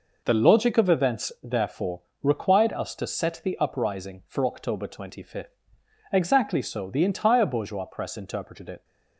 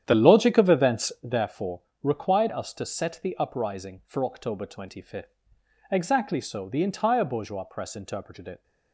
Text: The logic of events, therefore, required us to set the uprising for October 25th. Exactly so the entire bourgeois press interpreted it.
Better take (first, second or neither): first